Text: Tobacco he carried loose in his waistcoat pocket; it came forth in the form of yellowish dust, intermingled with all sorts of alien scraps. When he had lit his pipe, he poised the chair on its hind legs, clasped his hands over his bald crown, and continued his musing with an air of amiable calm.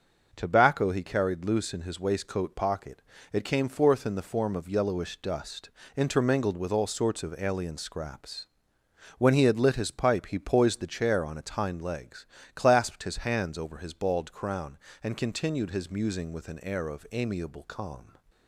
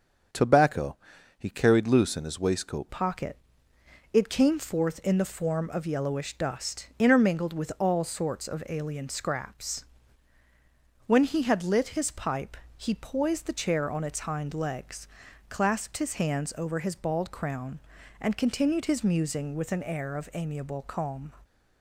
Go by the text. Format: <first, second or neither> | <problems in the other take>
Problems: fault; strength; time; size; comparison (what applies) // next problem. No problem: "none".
first | starts louder than the rest; until 1.7 s; 7 dB // pauses between "Tobacco" and "he"; at 0.9 s; 0.40 s long // changes voice at "pocket"; from 2.9 s on; 18.4 s long